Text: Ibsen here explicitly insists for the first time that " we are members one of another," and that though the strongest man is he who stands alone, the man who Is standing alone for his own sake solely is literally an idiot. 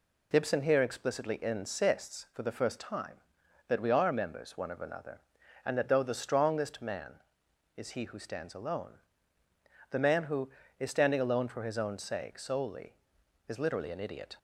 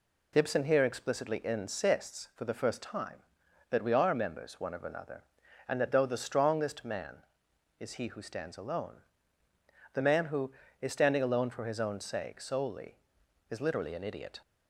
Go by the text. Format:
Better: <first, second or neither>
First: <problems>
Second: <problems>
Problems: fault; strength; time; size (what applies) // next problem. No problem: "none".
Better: neither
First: none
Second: none